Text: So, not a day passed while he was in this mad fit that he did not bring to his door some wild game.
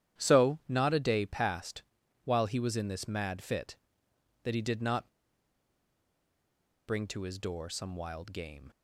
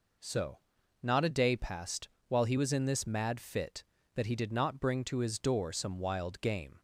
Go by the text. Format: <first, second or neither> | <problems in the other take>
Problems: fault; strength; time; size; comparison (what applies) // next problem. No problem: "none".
second | starts louder than the rest; strong; until 1.2 s; 10.5 dB // pauses between "passed" and "while"; at 1.8 s; 0.42 s long; slight in the second // pauses between "not" and "bring"; strong; at 5.0 s; 1.7 s long